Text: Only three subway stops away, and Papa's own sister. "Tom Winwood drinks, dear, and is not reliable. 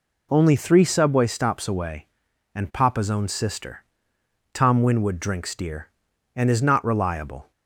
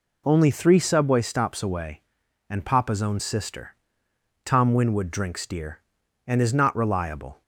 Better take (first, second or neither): neither